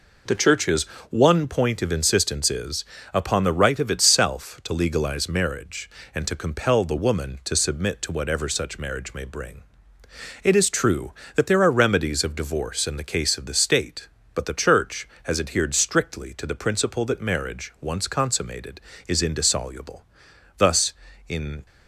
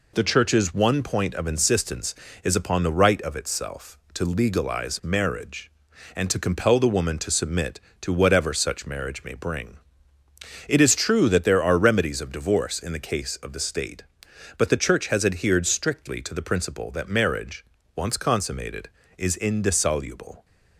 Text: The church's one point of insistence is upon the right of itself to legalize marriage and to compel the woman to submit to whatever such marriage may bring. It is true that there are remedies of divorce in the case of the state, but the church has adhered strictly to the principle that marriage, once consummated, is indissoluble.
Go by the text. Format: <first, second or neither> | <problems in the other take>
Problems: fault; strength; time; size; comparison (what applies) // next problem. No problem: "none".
second | pauses between "church's" and "one"; slight; at 0.8 s; 0.26 s long // pauses between "is" and "upon"; slight; at 2.8 s; 0.30 s long // goes on to say "Thus in"; noticeable; from 20.5 s on; 1.0 s long